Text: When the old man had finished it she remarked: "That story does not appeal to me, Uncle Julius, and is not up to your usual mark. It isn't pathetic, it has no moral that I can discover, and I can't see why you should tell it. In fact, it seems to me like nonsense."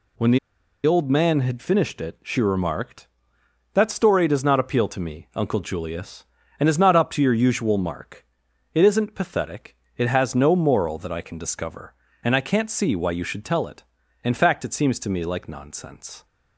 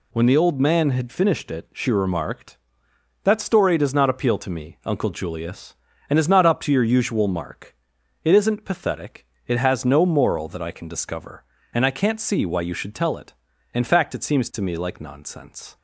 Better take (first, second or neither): second